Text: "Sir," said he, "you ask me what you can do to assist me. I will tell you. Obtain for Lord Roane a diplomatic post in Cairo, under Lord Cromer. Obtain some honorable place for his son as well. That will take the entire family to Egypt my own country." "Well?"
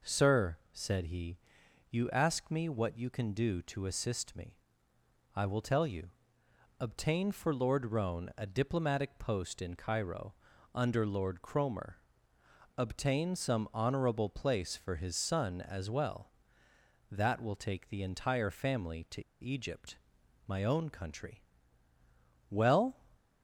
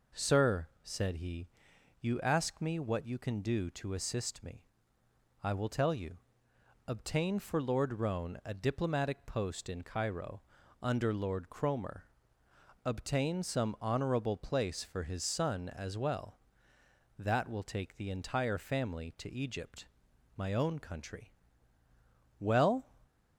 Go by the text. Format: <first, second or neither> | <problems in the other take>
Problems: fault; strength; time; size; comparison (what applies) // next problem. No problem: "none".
second | pauses between "to" and "Egypt"; slight; at 19.2 s; 0.18 s long // pauses between "Egypt" and "my"; noticeable; at 19.9 s; 0.50 s long; noticeable in the second